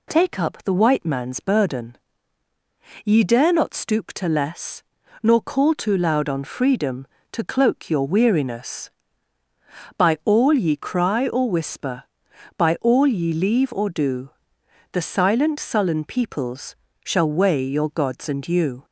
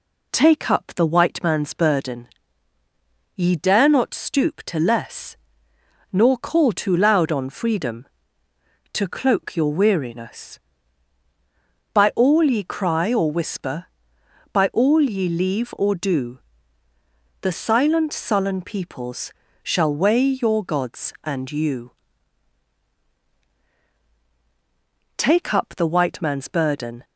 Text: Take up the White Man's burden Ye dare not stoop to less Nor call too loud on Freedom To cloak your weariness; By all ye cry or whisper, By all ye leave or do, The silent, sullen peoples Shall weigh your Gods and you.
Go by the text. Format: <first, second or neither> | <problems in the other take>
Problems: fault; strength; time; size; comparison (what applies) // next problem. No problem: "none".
first | pauses between "burden" and "Ye"; at 2.2 s; 1.0 s long; also in the first // pauses between "less" and "Nor"; noticeable; at 5.3 s; 0.76 s long; also in the first // pauses between "peoples" and "Shall"; slight; at 19.3 s; 0.32 s long; slight in the first // goes on to say "Take up the White Man's burden"; strong; from 25.1 s on; 1.8 s long